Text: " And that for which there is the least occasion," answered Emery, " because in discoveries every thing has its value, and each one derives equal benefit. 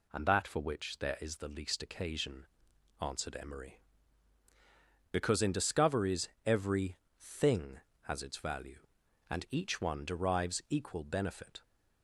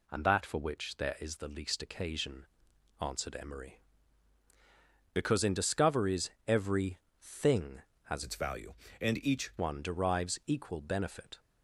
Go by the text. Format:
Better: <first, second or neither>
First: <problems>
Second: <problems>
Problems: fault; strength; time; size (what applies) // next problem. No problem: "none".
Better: first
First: pauses between "discoveries" and "every"; slight; at 6.2 s; 0.16 s long // pauses between "every" and "thing"; slight; at 6.9 s; 0.20 s long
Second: pauses between "discoveries" and "every"; slight; at 6.3 s; 0.16 s long // pauses between "every" and "thing"; slight; at 7.0 s; 0.20 s long // changes voice from "its" to "each"; from 8.2 to 9.5 s; 1.3 s long